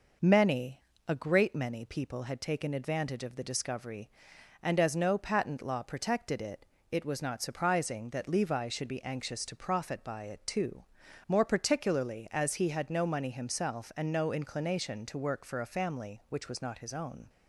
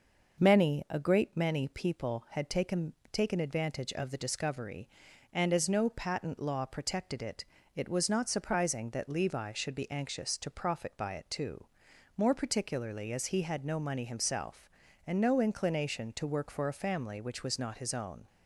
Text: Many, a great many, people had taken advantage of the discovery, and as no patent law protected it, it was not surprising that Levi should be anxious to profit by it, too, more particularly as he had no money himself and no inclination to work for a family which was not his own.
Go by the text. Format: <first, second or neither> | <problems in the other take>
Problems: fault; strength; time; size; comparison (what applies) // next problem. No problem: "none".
first | says "taken" twice; at 3.1 s